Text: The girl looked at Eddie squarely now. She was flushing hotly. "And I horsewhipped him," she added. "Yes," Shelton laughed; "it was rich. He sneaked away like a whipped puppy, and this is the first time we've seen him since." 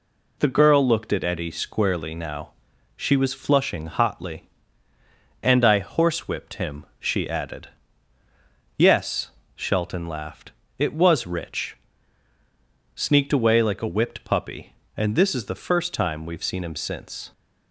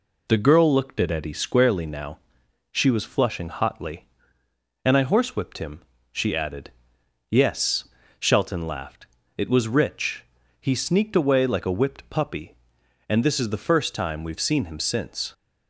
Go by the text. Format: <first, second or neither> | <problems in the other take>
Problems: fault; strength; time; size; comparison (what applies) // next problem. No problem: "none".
second | skips "He"; at 12.3 s